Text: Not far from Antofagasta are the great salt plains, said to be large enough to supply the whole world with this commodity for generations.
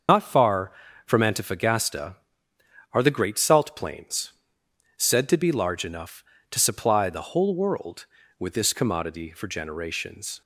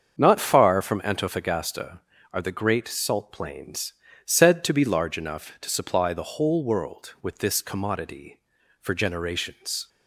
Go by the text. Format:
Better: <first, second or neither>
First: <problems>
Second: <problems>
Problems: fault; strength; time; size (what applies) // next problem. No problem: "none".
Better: second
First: loses the start of "Not"; at 0.0 s; 100 ms // starts louder than the rest; until 1.4 s; 6.5 dB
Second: starts louder than the rest; until 1.1 s; 7 dB